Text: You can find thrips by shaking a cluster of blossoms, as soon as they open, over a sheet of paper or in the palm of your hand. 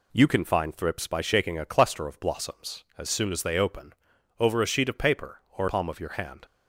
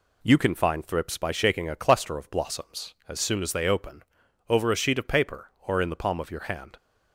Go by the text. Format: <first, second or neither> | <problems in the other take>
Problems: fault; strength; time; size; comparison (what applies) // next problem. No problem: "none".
second | skips "in the"; at 5.6 s